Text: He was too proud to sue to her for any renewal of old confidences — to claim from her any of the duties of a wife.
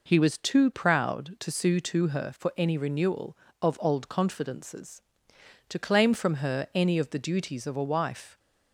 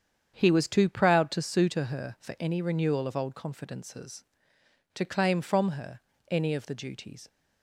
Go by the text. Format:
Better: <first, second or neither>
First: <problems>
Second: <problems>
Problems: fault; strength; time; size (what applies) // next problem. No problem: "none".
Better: first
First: none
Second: starts louder than the rest; strong; until 1.3 s; 8 dB // pauses between "her" and "any"; slight; at 6.0 s; 0.28 s long // stops before "of a wife"; at 7.2 s